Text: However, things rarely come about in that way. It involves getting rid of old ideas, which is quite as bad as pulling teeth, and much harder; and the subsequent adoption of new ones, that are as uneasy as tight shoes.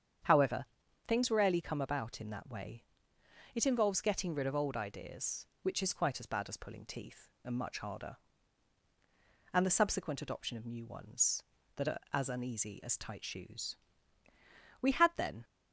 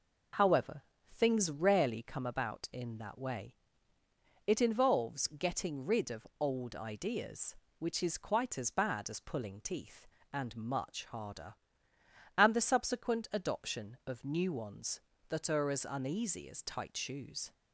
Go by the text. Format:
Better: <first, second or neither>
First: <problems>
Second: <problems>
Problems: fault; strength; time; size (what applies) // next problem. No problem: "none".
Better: second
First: starts louder than the rest; strong; until 1.6 s; 8 dB // goes on to say "We had then"; noticeable; from 14.8 s on; 0.62 s long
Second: none